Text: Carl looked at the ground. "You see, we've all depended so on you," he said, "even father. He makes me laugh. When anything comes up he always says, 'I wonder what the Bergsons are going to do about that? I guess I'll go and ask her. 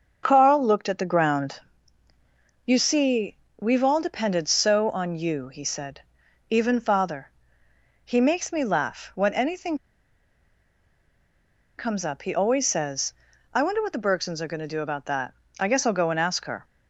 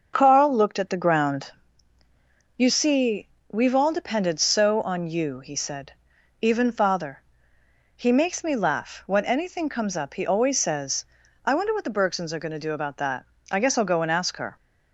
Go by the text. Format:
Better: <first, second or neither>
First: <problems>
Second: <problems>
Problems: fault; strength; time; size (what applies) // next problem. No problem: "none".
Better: second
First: starts louder than the rest; until 1.2 s; 6.5 dB // pauses between "anything" and "comes"; strong; at 9.7 s; 2.0 s long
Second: starts louder than the rest; until 1.1 s; 6.5 dB